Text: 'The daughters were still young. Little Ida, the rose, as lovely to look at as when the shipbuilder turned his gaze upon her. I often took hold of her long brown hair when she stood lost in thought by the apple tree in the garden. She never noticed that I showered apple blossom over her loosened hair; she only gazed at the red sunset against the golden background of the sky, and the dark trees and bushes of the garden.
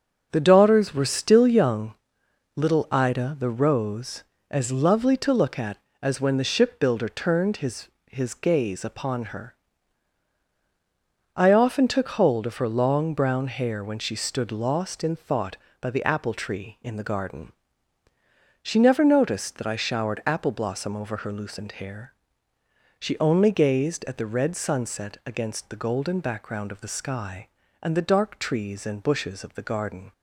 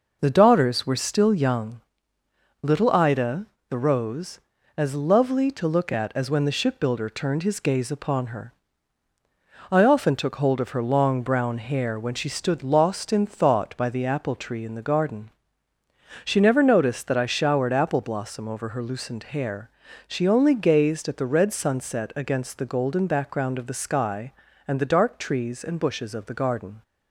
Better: second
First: starts louder than the rest; until 1.3 s; 6 dB // says "his" twice; at 8.0 s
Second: none

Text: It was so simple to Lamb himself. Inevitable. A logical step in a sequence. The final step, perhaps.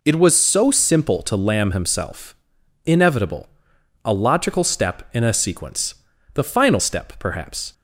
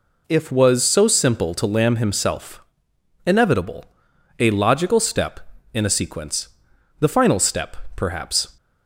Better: first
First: none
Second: says "If" for "It"; at 0.2 s

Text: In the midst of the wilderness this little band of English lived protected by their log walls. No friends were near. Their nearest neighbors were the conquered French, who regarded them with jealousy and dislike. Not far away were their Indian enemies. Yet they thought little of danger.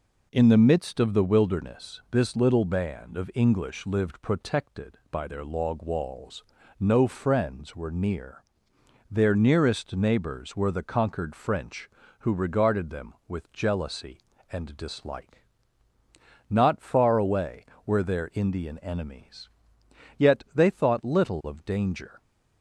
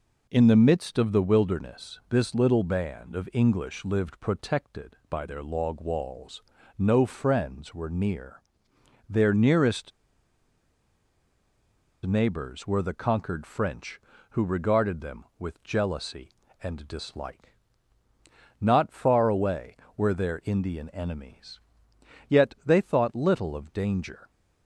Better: first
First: none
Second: pauses between "nearest" and "neighbors"; strong; at 9.9 s; 2.1 s long

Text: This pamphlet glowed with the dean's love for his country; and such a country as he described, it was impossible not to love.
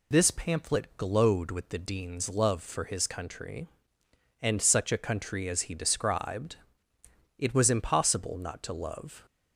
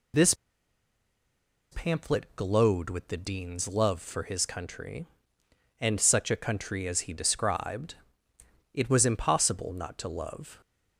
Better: first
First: none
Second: pauses between "This" and "pamphlet"; strong; at 0.3 s; 1.3 s long

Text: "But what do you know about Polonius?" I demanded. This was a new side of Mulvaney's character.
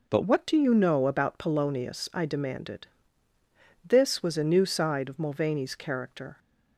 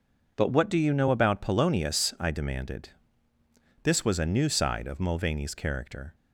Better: second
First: changes voice at "what"; from 0.2 s on; 6.1 s long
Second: none

